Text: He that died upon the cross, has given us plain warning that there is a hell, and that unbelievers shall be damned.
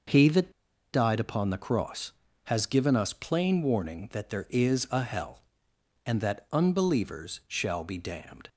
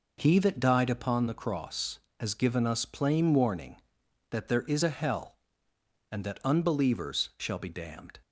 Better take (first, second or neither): second